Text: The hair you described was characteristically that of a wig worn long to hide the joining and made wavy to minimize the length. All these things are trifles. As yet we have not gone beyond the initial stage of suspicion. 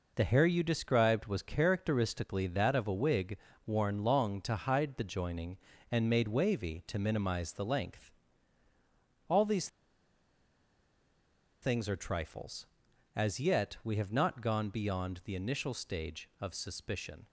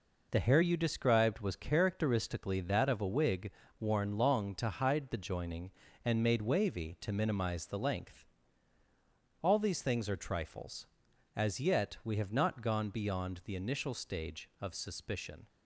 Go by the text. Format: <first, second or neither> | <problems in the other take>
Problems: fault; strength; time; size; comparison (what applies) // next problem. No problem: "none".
second | pauses between "wig" and "worn"; slight; at 3.3 s; 0.30 s long; slight in the second // pauses between "these" and "things"; strong; at 9.6 s; 1.9 s long